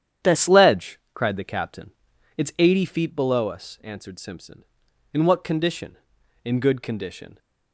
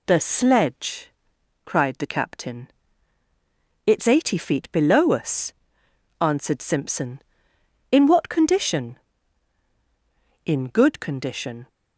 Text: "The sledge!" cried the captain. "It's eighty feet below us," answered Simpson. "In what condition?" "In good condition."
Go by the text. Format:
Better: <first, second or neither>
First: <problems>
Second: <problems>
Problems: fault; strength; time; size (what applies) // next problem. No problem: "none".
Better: second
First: starts louder than the rest; strong; until 1.4 s; 9.5 dB // changes voice at "sledge"; from 0.3 s on; 7.0 s long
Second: none